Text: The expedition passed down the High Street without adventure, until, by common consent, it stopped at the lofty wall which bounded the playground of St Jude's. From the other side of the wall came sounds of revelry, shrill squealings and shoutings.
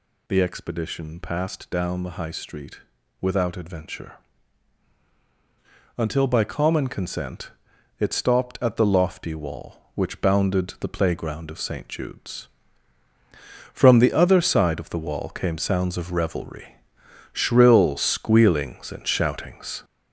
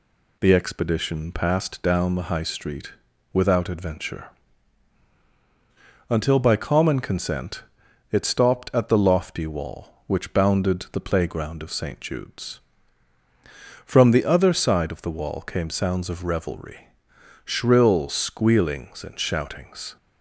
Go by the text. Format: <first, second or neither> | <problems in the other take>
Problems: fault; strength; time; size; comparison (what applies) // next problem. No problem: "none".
second | gets louder; noticeable; throughout; 5.5 dB // pauses between "Street" and "without"; at 2.8 s; 0.40 s long; also in the second